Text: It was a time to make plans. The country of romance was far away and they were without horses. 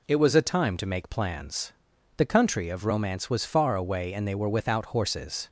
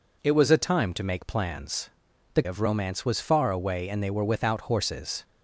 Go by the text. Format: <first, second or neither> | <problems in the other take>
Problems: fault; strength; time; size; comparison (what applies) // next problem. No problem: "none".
first | skips "country"; at 2.4 s